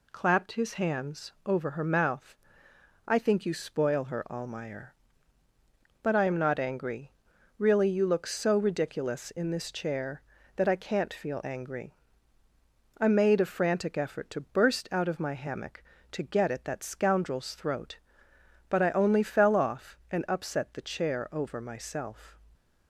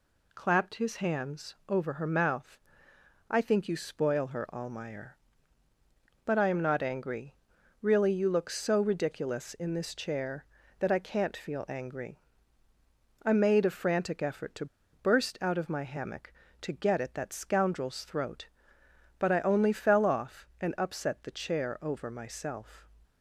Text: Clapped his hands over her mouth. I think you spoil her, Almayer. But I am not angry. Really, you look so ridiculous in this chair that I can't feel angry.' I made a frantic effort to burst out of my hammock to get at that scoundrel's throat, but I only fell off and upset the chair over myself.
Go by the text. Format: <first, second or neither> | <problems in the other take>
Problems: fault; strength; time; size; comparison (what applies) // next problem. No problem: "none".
first | pauses between "to" and "burst"; slight; at 14.6 s; 0.27 s long